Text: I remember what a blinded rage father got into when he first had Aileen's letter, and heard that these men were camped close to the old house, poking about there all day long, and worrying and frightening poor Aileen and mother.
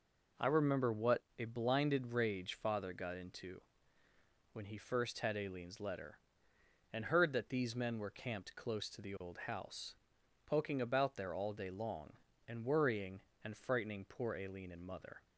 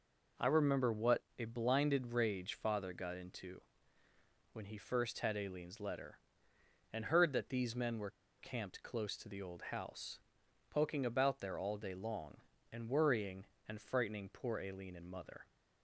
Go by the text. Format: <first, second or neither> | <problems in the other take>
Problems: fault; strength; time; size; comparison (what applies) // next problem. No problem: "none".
first | pauses between "what" and "a"; slight; at 1.2 s; 0.18 s long; slight in the first // pauses between "into" and "when"; noticeable; at 3.6 s; 0.90 s long; noticeable in the first // pauses between "were" and "camped"; slight; at 8.0 s; 0.29 s long